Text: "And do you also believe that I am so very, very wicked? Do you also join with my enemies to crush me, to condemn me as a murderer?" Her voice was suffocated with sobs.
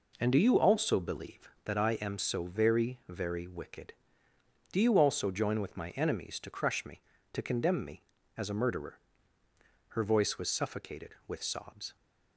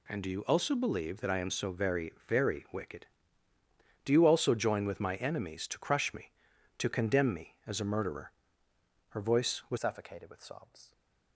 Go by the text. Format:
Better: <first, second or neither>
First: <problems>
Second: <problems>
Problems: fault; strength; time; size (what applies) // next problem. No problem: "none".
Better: first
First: none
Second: changes voice at "suffocated"; from 9.7 s on; 1.2 s long